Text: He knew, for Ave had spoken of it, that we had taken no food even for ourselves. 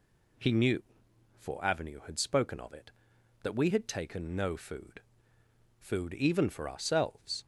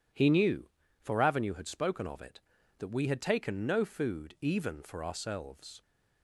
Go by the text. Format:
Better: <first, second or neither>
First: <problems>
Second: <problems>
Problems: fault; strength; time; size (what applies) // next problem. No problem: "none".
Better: second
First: says "food" twice; at 5.7 s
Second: none